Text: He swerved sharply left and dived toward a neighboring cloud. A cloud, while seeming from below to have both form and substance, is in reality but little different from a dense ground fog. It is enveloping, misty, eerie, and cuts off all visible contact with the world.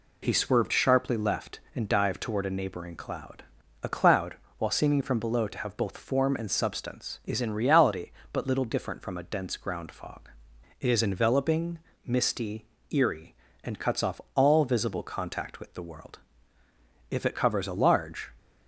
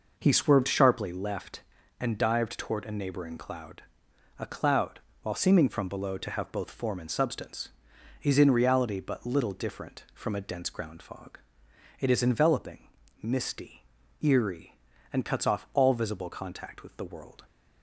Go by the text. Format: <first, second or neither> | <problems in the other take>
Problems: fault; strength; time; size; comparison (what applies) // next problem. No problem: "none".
second | goes on to say "If it covers a large"; noticeable; from 17.0 s on; 1.2 s long